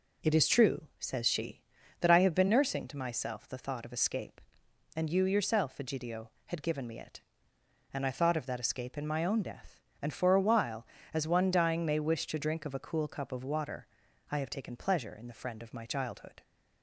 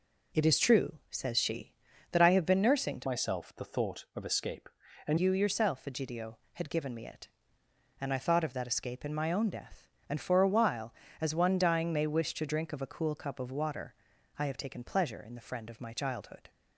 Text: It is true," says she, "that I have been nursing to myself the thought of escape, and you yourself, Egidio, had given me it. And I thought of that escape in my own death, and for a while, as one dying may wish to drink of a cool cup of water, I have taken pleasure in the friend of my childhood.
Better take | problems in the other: first | changes voice from "myself" to "and"; from 3.0 to 5.1 s; 2.1 s long

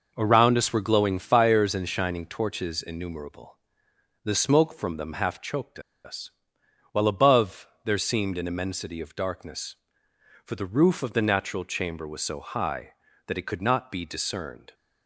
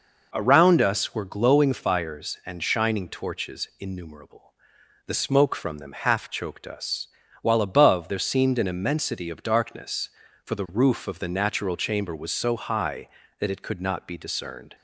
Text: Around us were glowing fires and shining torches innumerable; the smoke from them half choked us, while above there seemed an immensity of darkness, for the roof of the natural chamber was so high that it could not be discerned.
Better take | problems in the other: second | pauses between "choked" and "us"; slight; at 5.7 s; 0.25 s long // pauses between "above" and "there"; slight; at 7.6 s; 0.20 s long

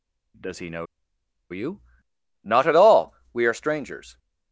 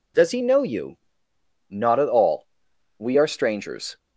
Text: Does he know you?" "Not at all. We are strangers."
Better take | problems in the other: second | pauses between "know" and "you"; noticeable; at 0.8 s; 0.65 s long

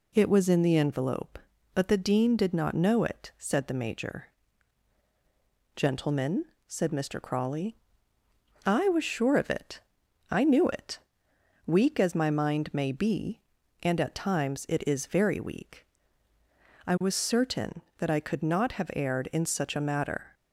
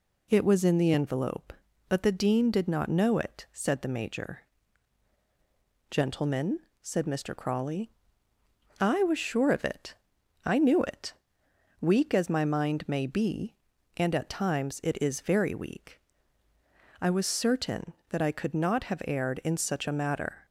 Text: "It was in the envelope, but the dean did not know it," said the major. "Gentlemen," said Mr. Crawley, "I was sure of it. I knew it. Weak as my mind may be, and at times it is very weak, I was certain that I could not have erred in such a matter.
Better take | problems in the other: neither | none

